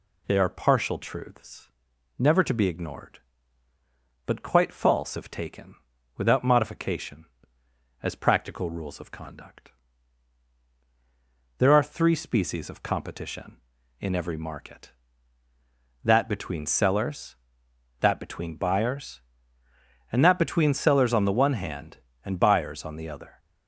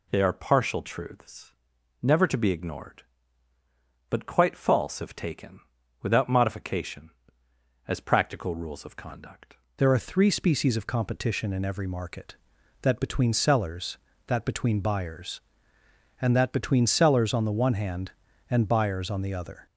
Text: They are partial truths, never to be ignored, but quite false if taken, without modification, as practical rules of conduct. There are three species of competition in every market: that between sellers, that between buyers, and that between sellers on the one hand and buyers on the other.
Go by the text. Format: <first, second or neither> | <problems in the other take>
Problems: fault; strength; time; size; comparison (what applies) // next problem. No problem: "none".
first | changes voice at "There"; from 9.7 s on; 9.9 s long